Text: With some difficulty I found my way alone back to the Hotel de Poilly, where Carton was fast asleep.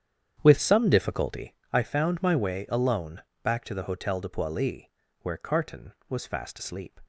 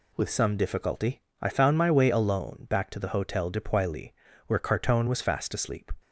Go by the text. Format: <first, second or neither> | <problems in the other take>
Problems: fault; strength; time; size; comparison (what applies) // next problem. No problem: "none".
second | starts louder than the rest; strong; until 1.5 s; 9 dB // pauses between "difficulty" and "I"; slight; at 1.5 s; 0.16 s long; slight in the second // pauses between "alone" and "back"; slight; at 3.2 s; 0.20 s long